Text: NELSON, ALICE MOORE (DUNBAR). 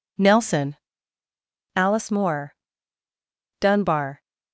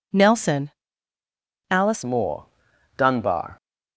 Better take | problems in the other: first | changes voice at "MOORE"; from 2.0 s on; 1.5 s long

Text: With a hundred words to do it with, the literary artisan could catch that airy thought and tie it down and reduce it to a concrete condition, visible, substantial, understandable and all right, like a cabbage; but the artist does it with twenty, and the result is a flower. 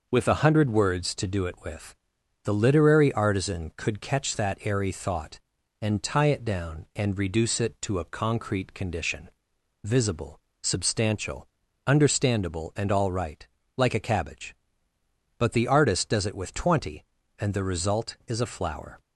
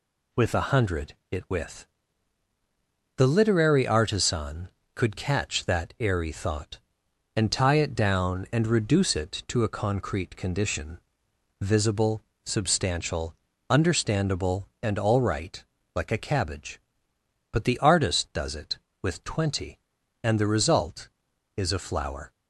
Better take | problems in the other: first | skips "words to do"; at 1.2 s

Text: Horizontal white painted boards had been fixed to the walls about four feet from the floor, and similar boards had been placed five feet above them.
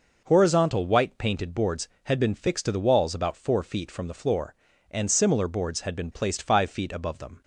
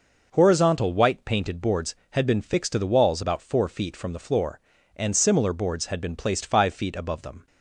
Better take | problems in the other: neither | none

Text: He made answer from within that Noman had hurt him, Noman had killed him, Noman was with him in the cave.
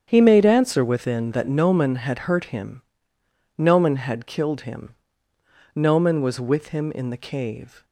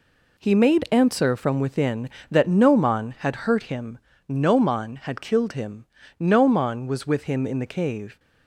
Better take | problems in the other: second | starts louder than the rest; strong; until 1.0 s; 8 dB // skips "from"; at 0.8 s

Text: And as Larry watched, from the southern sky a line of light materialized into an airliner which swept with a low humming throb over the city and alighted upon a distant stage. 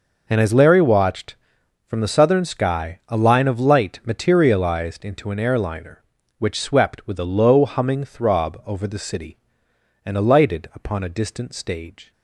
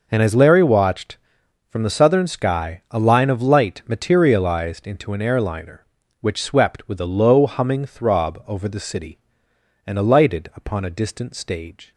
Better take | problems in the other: neither | none

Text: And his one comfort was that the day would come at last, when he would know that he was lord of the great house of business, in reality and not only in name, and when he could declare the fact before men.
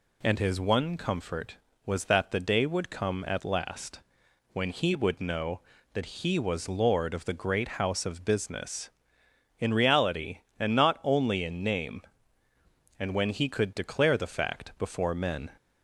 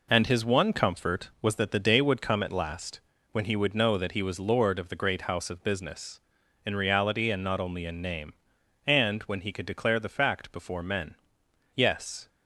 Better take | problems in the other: first | goes on to say "Yes"; from 11.7 s on; 0.54 s long

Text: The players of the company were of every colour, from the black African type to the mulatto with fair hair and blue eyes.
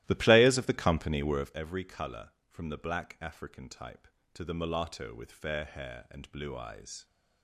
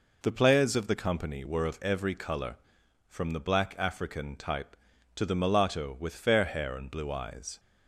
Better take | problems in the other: second | starts louder than the rest; strong; until 1.6 s; 15 dB

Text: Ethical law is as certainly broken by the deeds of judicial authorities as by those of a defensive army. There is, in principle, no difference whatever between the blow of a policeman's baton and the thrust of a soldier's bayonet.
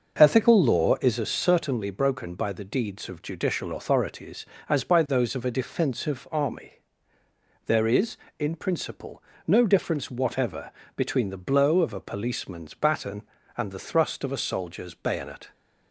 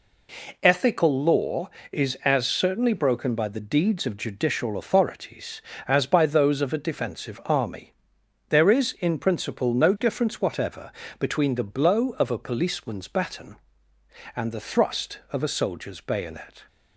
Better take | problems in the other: second | starts louder than the rest; noticeable; until 1.3 s; 6 dB // pauses between "whatever" and "between"; slight; at 10.7 s; 0.26 s long; slight in the second

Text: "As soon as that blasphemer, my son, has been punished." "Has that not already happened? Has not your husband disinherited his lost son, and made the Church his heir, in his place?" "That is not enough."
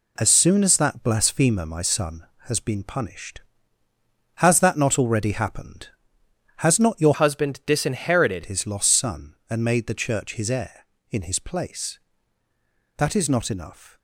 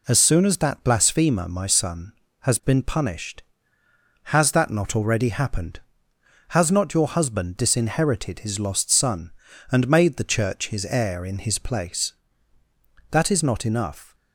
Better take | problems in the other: second | changes voice from "husband" to "disinherited"; from 7.1 to 8.4 s; 1.3 s long

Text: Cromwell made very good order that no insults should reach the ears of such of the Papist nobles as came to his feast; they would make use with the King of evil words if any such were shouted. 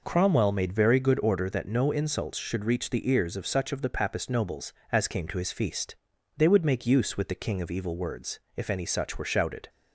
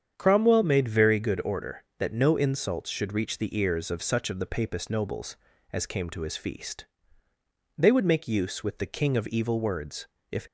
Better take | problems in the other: first | starts louder than the rest; strong; until 1.1 s; 8 dB // pauses between "words" and "if"; slight; at 10.0 s; 0.24 s long; slight in the first // stops before "any such were shouted"; at 10.4 s

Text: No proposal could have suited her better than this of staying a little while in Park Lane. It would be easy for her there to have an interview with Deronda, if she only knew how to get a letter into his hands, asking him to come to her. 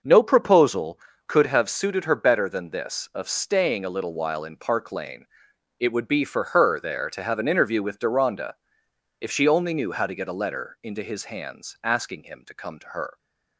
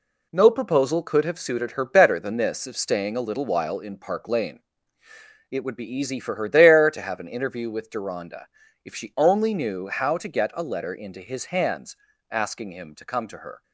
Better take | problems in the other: second | skips "easy"; at 6.2 s

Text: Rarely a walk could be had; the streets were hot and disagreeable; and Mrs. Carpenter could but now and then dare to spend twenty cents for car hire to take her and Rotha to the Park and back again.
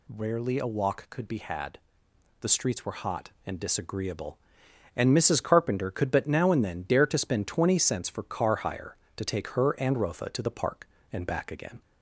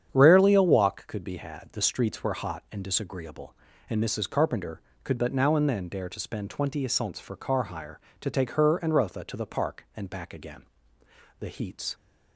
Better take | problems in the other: first | starts louder than the rest; strong; until 1.1 s; 8.5 dB // goes on to say "The heats"; from 11.3 s on; 0.56 s long

